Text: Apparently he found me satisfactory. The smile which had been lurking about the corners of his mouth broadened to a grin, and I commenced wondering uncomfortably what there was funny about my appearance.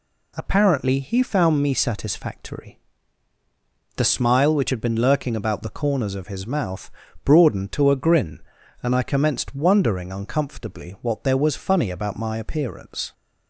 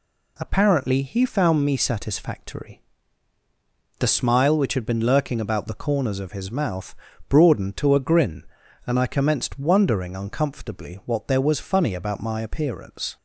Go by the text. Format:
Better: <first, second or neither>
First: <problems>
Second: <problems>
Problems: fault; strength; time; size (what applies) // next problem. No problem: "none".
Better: neither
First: pauses between "mouth" and "broadened"; slight; at 6.9 s; 0.34 s long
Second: pauses between "mouth" and "broadened"; slight; at 6.9 s; 0.34 s long